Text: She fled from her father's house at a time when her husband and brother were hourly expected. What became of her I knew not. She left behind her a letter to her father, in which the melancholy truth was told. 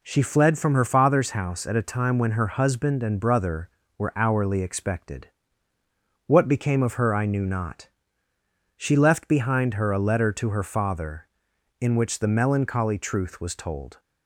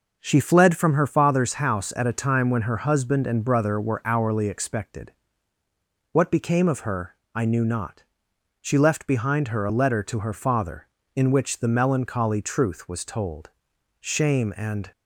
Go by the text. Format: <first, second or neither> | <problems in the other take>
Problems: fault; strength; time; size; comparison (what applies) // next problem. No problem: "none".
first | pauses between "her" and "I"; slight; at 7.1 s; 0.18 s long // goes on to say "Shame and"; noticeable; from 14.0 s on; 0.90 s long